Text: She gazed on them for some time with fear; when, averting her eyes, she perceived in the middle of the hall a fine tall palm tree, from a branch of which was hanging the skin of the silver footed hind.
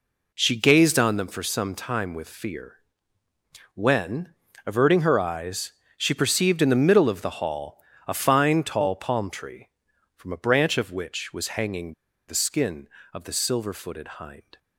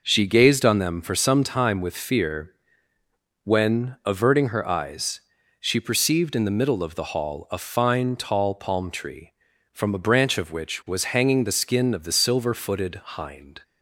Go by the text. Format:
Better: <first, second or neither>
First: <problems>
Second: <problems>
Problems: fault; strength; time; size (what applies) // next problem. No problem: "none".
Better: second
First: pauses between "hall" and "a"; slight; at 7.8 s; 0.24 s long // pauses between "hanging" and "the"; slight; at 11.9 s; 0.35 s long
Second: none